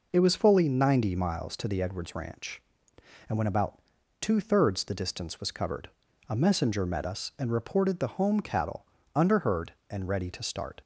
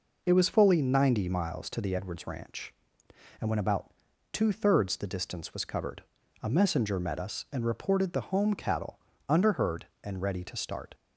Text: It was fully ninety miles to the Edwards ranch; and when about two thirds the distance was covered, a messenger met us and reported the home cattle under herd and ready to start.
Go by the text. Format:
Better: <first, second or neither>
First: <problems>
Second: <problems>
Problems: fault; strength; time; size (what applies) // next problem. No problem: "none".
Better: neither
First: pauses between "about" and "two"; at 3.7 s; 0.40 s long // pauses between "cattle" and "under"; slight; at 8.8 s; 0.28 s long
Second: pauses between "about" and "two"; at 3.9 s; 0.40 s long // pauses between "cattle" and "under"; slight; at 8.9 s; 0.28 s long